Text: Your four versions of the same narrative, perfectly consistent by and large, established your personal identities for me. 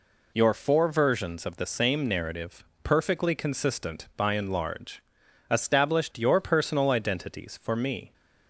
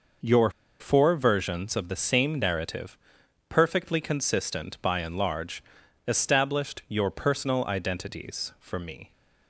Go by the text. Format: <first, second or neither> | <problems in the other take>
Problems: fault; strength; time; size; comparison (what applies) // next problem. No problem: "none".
first | pauses between "Your" and "four"; slight; at 0.5 s; 0.28 s long